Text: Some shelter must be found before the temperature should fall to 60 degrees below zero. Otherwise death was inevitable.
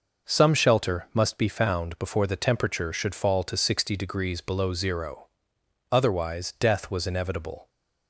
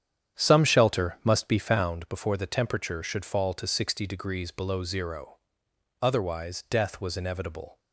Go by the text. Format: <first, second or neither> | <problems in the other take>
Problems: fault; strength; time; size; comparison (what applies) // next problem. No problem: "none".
first | starts louder than the rest; strong; until 2.0 s; 9.5 dB